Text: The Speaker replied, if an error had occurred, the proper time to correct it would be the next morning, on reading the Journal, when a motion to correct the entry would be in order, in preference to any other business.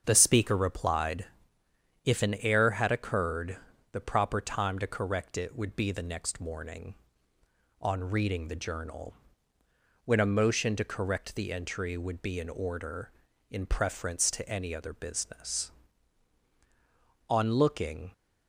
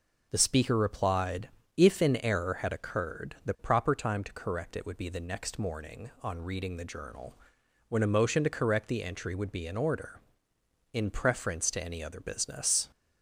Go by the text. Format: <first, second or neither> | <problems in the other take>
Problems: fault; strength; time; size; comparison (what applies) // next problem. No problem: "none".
second | starts louder than the rest; strong; until 1.0 s; 7.5 dB // goes on to say "On looking"; noticeable; from 17.2 s on; 0.84 s long